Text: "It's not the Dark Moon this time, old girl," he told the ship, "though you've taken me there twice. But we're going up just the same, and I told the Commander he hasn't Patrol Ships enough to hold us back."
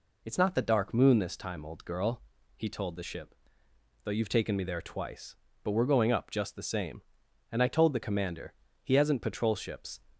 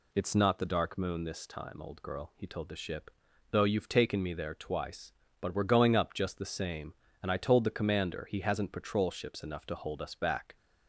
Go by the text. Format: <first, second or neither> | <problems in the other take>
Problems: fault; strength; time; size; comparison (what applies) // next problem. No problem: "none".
second | pauses between "Commander" and "he"; slight; at 8.5 s; 0.30 s long // stops before "enough to hold us back"; at 10.1 s